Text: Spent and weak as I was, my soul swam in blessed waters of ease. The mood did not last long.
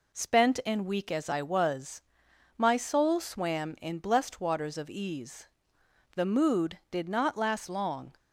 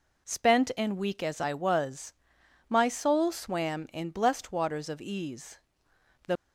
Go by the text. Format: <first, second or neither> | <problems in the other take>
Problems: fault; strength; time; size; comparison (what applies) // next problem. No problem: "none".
first | stops before "mood did not last long"; at 6.3 s